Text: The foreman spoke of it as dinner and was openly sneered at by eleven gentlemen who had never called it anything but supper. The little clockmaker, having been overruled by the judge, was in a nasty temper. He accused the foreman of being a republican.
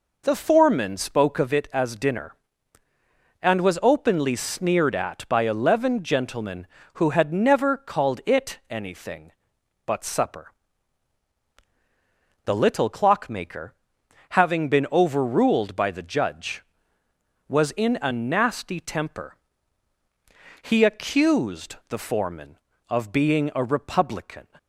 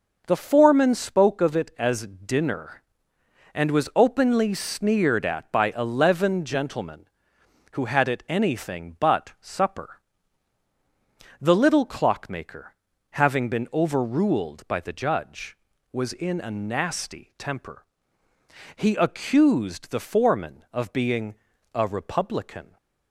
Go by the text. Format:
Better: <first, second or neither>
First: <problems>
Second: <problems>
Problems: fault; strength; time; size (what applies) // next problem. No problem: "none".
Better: first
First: none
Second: skips "never called"; at 8.0 s // pauses between "being" and "a"; at 21.3 s; 0.40 s long